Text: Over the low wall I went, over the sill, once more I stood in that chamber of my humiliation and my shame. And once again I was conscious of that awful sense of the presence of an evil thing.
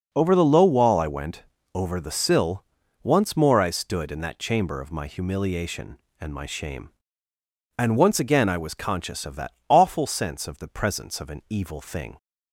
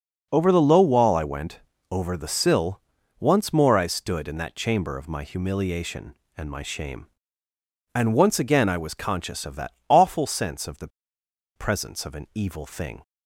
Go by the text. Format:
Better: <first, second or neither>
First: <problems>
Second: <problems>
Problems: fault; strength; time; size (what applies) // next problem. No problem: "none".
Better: first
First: pauses between "that" and "awful"; slight; at 9.5 s; 0.16 s long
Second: pauses between "that" and "awful"; slight; at 9.7 s; 0.16 s long // pauses between "the" and "presence"; noticeable; at 10.8 s; 0.67 s long